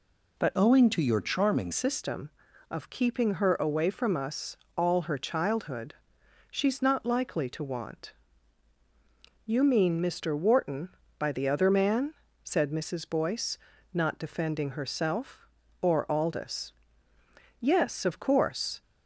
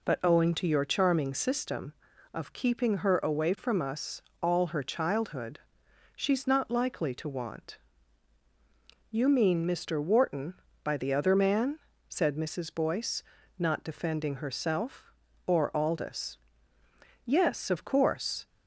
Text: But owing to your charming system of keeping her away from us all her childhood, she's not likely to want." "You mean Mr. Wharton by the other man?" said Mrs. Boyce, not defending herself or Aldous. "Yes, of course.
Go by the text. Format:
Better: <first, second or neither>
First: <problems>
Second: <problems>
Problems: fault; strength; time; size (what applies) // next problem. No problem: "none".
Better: second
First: changes voice from "owing" to "charming"; from 0.5 to 1.7 s; 1.2 s long // pauses between "us" and "all"; slight; at 4.5 s; 0.18 s long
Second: pauses between "us" and "all"; slight; at 4.2 s; 0.18 s long